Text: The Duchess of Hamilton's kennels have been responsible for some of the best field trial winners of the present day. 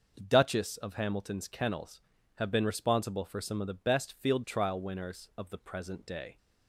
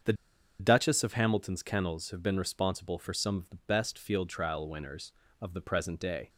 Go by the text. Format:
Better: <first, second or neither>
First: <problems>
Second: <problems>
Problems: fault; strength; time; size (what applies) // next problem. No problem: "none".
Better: first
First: starts louder than the rest; noticeable; until 1.1 s; 6 dB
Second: starts louder than the rest; until 1.5 s; 7 dB // pauses between "The" and "Duchess"; noticeable; at 0.1 s; 0.46 s long